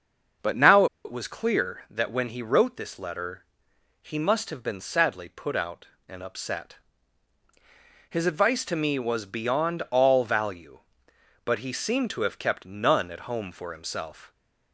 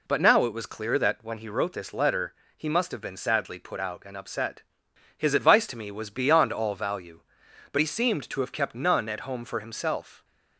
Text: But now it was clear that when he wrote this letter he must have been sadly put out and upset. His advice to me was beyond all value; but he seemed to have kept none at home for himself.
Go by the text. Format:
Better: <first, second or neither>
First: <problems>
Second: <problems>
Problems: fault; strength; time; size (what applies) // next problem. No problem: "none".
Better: second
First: starts louder than the rest; until 1.6 s; 6.5 dB // pauses between "now" and "it"; slight; at 0.8 s; 0.19 s long // pauses between "letter" and "he"; noticeable; at 3.4 s; 0.60 s long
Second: pauses between "letter" and "he"; slight; at 2.3 s; 0.24 s long